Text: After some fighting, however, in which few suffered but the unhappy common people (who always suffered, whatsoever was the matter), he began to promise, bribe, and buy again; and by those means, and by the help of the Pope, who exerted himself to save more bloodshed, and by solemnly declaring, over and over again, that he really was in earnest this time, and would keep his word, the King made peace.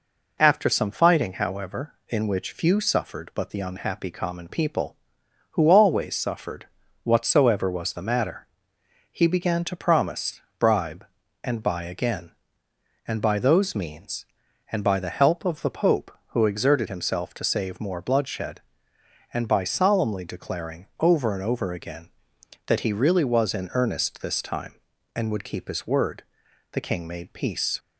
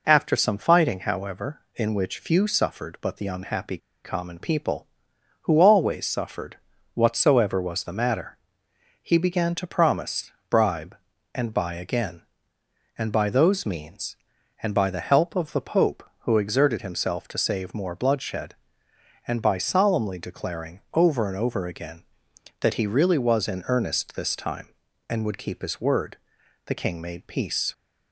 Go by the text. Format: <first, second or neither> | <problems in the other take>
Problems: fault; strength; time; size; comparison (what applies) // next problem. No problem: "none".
first | pauses between "unhappy" and "common"; slight; at 3.7 s; 0.27 s long